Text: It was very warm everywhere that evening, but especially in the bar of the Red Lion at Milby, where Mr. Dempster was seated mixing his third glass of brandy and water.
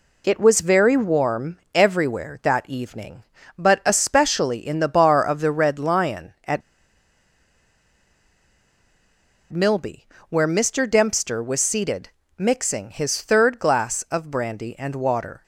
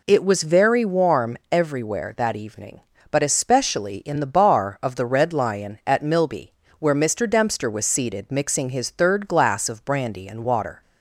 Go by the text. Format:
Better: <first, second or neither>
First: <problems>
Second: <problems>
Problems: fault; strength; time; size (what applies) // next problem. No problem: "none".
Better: second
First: pauses between "at" and "Milby"; strong; at 6.6 s; 2.9 s long // pauses between "seated" and "mixing"; slight; at 12.0 s; 0.28 s long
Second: none